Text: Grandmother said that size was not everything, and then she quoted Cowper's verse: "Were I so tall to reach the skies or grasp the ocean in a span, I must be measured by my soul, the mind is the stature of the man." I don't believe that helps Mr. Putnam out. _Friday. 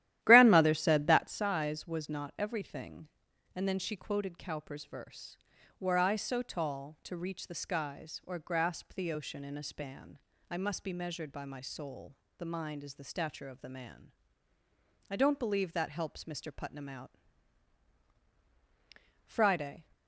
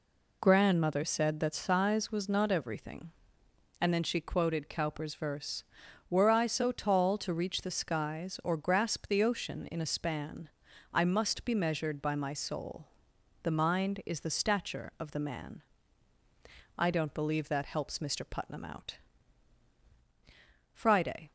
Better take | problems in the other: second | starts louder than the rest; strong; until 1.4 s; 13 dB

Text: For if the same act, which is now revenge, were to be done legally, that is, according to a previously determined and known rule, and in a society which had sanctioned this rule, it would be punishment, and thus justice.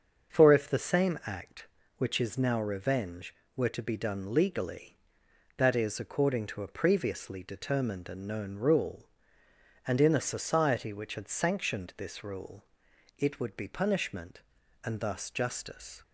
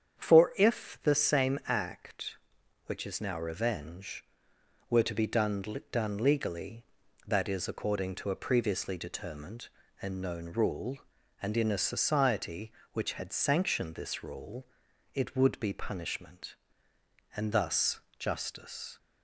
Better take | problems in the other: first | starts louder than the rest; strong; until 1.2 s; 8 dB; also in the first // says "done" twice; at 5.9 s // pauses between "thus" and "justice"; slight; at 17.9 s; 0.18 s long

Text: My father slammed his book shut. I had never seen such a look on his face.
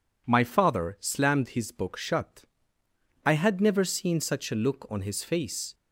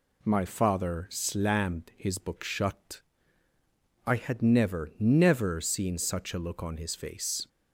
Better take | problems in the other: first | says "never" twice; at 4.9 s

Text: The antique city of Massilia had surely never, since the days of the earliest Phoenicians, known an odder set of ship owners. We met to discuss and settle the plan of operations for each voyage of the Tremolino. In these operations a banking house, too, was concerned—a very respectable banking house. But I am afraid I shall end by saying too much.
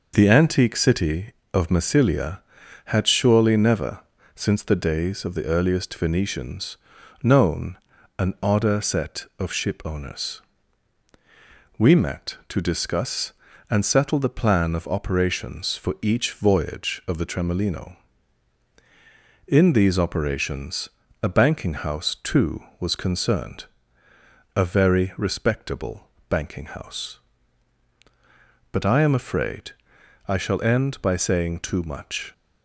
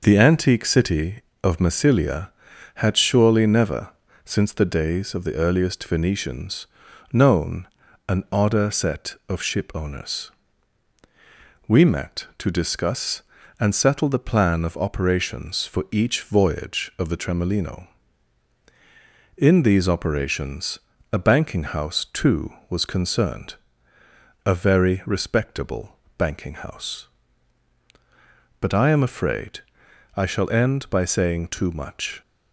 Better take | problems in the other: neither | pauses between "known" and "an"; the same in both // pauses between "operations" and "a"; slight; the same in both // pauses between "respectable" and "banking"; slight; the same in both // pauses between "afraid" and "I"; noticeable; the same in both

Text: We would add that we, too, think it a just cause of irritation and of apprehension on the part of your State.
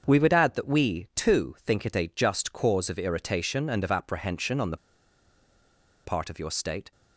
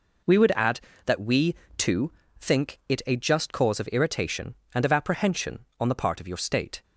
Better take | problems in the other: second | starts louder than the rest; until 1.0 s; 7 dB // pauses between "the" and "part"; strong; at 4.7 s; 1.2 s long

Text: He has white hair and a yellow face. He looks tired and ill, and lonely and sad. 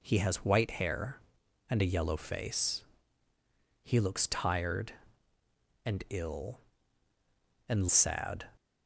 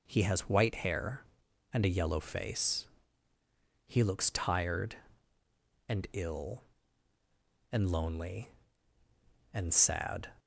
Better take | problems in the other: second | skips "lonely and"; at 7.8 s

